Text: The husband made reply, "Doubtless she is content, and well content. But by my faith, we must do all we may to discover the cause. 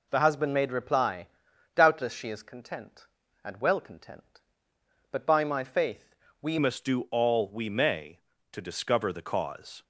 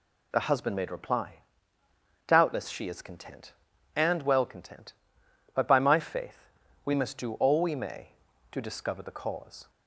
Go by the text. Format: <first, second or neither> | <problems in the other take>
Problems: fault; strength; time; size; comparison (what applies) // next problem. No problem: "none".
second | changes voice at "must"; from 6.5 s on; 3.3 s long